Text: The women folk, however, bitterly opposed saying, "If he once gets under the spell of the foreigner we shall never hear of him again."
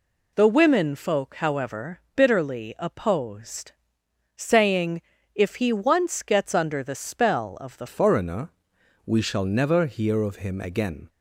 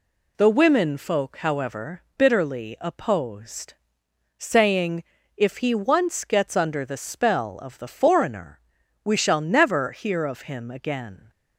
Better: second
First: pauses between "opposed" and "saying"; noticeable; at 3.7 s; 0.62 s long // changes voice at "foreigner"; from 7.8 s on; 3.2 s long // pauses between "foreigner" and "we"; noticeable; at 8.5 s; 0.52 s long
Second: pauses between "opposed" and "saying"; noticeable; at 3.7 s; 0.62 s long // pauses between "foreigner" and "we"; noticeable; at 8.5 s; 0.46 s long

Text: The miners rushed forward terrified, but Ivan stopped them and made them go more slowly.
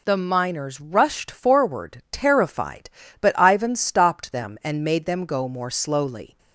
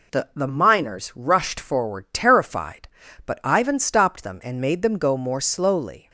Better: first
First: none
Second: says "The" twice; at 0.3 s

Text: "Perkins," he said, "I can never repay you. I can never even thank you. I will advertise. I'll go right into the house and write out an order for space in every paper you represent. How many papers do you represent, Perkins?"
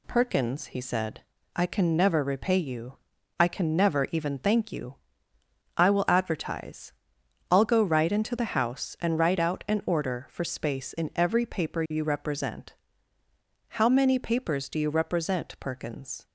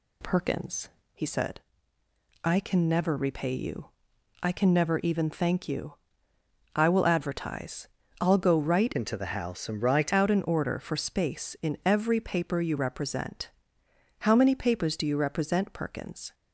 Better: first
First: none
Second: changes voice from "into" to "write"; from 8.9 to 10.1 s; 1.2 s long

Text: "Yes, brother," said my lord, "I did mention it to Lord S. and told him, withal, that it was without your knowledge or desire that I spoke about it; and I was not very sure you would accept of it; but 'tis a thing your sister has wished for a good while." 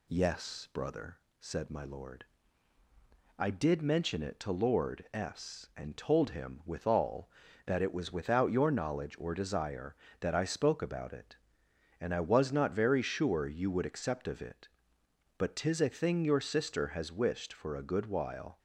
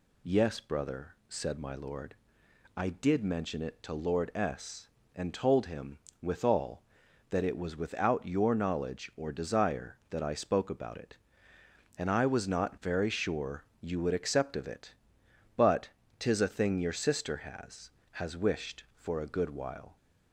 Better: first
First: none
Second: pauses between "sure" and "you"; slight; at 13.6 s; 0.16 s long // pauses between "but" and "tis"; slight; at 15.8 s; 0.30 s long // says "has" twice; at 18.1 s

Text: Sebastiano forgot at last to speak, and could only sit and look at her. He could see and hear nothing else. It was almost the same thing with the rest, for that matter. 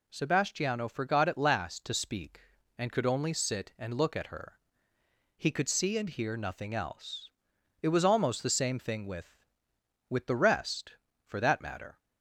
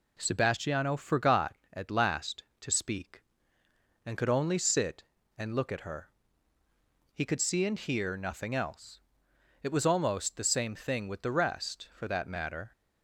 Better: second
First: says "with" twice; at 10.0 s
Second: none

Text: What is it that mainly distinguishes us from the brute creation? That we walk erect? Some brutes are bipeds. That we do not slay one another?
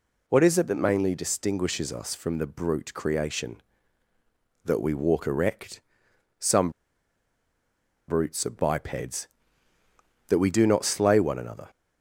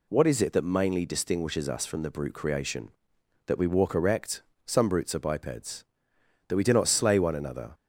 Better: second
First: pauses between "Some" and "brutes"; strong; at 6.7 s; 1.3 s long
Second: none

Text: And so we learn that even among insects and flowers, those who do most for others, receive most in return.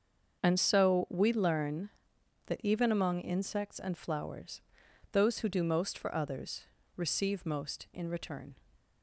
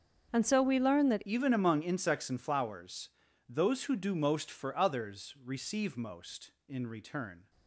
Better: first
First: starts louder than the rest; until 1.4 s; 6.5 dB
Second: starts louder than the rest; until 1.3 s; 7 dB // changes voice at "even"; from 1.2 s on; 6.2 s long

